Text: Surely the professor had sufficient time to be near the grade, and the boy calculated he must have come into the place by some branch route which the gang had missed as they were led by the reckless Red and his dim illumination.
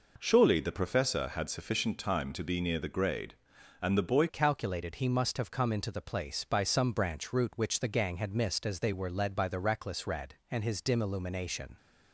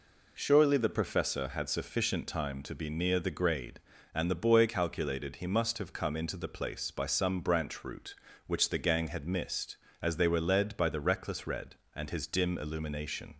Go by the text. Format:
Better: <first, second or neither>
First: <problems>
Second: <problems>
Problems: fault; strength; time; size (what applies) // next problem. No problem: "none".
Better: second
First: changes voice at "calculated"; from 4.2 s on; 7.5 s long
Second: none